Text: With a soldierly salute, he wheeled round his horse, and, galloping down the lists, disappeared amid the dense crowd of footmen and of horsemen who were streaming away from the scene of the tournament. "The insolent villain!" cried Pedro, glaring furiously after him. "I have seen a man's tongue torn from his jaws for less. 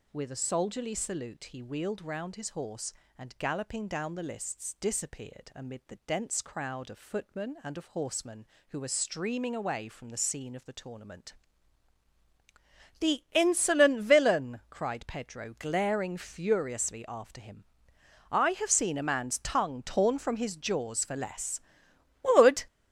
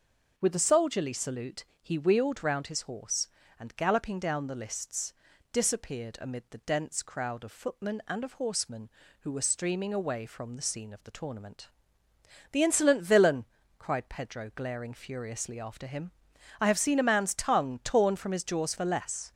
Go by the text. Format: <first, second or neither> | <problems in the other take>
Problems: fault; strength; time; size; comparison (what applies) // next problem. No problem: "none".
second | goes on to say "Would"; slight; from 22.2 s on; 0.42 s long